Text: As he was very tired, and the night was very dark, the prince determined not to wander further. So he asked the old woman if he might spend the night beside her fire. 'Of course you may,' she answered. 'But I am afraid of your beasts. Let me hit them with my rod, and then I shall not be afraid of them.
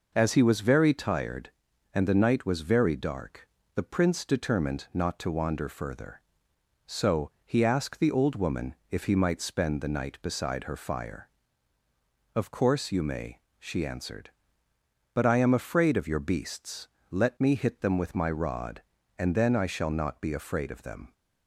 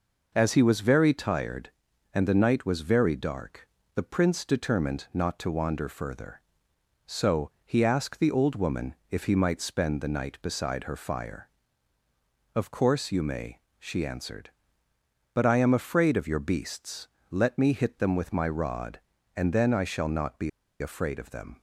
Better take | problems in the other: first | pauses between "woman" and "if"; slight; at 8.9 s; 0.16 s long; slight in the first // pauses between "be" and "afraid"; slight; at 20.4 s; 0.30 s long

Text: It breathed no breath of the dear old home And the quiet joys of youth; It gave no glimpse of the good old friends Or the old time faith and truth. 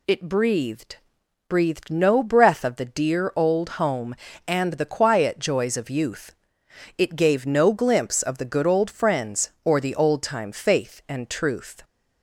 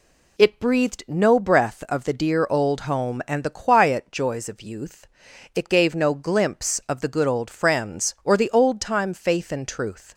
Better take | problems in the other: second | says "breathed" twice; at 1.4 s

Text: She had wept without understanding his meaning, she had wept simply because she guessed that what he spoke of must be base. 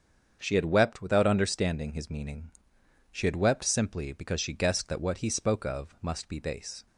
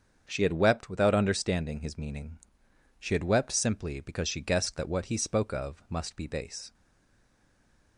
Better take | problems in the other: first | starts louder than the rest; strong; until 1.3 s; 7 dB; strong in the first // stays silent after the last word; noticeable; from 6.7 s on; 1.2 s long

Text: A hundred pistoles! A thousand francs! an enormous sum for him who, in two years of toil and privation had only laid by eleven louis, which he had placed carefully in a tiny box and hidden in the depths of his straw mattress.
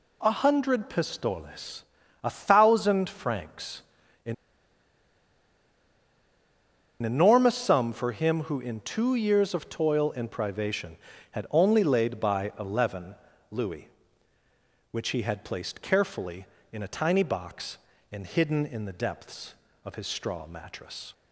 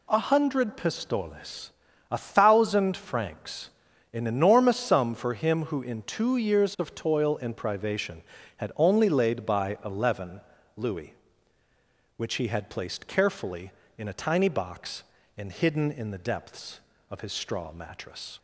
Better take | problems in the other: second | pauses between "an" and "enormous"; strong; at 4.3 s; 2.6 s long // pauses between "eleven" and "louis"; at 13.1 s; 0.38 s long; also in the second

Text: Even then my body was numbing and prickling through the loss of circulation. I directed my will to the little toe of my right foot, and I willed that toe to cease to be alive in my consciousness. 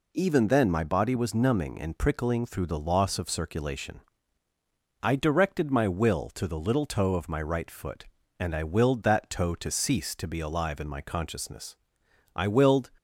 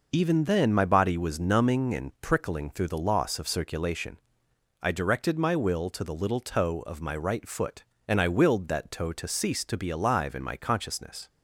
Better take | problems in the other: second | goes on to say "I willed"; from 12.3 s on; 0.56 s long

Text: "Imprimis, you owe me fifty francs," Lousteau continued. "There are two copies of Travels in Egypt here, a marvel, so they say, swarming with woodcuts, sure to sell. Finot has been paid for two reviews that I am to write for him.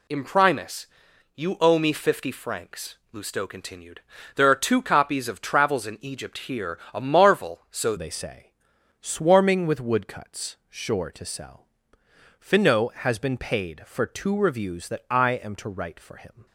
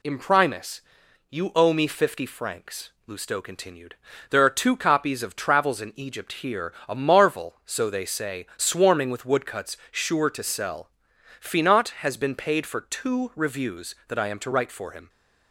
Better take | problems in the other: second | changes voice at "they"; from 7.9 s on; 8.5 s long

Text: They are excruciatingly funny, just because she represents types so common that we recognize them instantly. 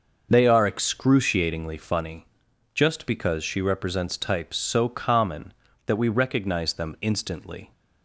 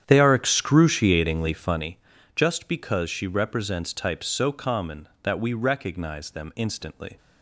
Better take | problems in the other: first | starts louder than the rest; strong; until 1.9 s; 9.5 dB

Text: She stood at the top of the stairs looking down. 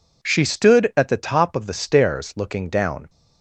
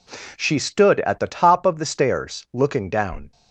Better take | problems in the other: neither | none

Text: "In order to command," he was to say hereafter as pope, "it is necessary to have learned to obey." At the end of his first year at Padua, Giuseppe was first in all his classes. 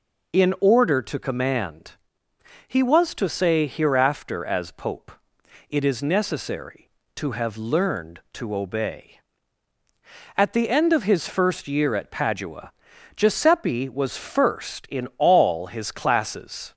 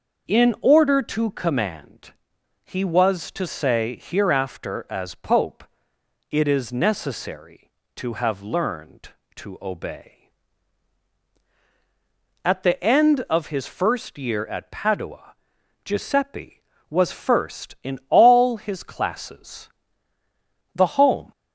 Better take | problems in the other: first | starts louder than the rest; until 1.3 s; 6 dB // goes on to say "The home"; from 20.7 s on; 0.56 s long

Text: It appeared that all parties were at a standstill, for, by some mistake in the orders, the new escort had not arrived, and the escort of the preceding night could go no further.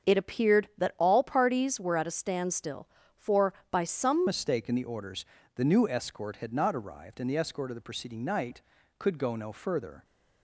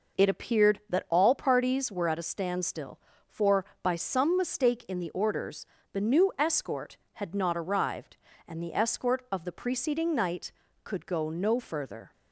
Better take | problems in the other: second | starts louder than the rest; until 1.1 s; 6.5 dB // changes voice at "mistake"; from 4.2 s on; 5.8 s long

